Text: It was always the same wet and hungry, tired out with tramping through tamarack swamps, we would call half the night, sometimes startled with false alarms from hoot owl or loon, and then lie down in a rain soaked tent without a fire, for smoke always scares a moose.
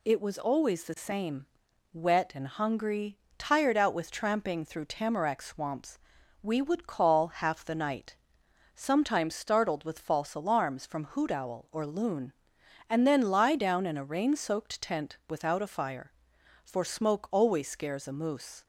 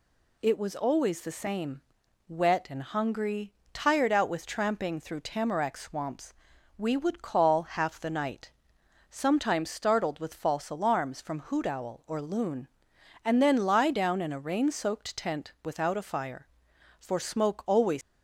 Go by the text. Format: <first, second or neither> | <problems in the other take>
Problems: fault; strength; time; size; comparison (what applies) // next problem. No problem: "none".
first | pauses between "same" and "wet"; noticeable; at 1.8 s; 0.48 s long; noticeable in the first // stops before "scares a moose"; at 18.0 s